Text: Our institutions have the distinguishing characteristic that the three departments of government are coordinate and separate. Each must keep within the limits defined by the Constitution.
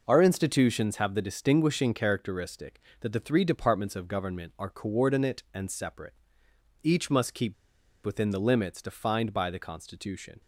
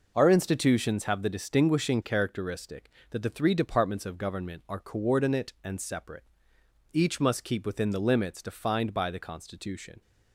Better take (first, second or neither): second